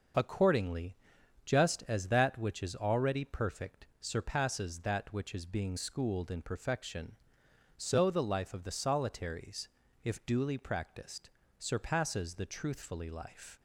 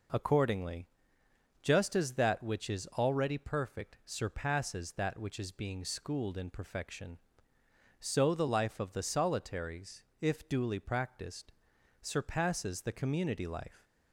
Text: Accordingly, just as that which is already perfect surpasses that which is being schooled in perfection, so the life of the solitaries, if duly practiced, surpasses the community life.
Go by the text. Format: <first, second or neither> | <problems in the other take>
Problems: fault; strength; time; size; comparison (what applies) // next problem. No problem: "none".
second | starts louder than the rest; noticeable; until 1.6 s; 6 dB // says "truthfully" for "community"; at 12.4 s